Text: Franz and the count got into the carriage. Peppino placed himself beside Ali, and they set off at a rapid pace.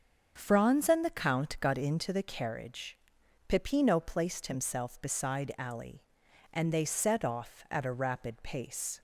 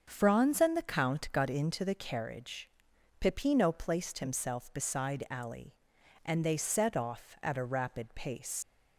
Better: first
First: starts louder than the rest; until 1.3 s; 7 dB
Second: starts louder than the rest; until 1.0 s; 7 dB // leaves "pace" unfinished; at 8.6 s; 100 ms

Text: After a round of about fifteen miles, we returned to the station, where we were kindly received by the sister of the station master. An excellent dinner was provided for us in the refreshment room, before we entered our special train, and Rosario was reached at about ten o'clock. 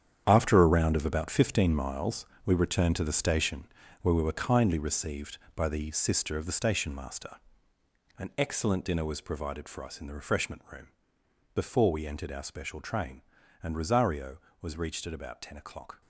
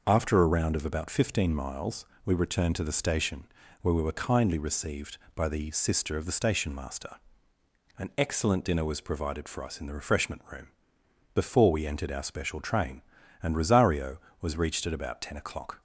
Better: second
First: gets quieter; strong; throughout; 11.5 dB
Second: none

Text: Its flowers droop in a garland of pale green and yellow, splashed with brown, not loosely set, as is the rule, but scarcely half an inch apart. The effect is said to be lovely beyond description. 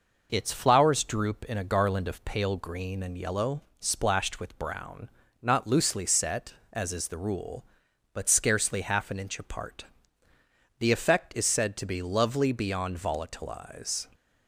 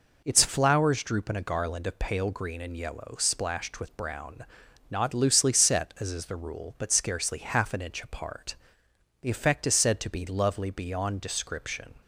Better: second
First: says "volatilize" for "description"; at 12.9 s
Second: none

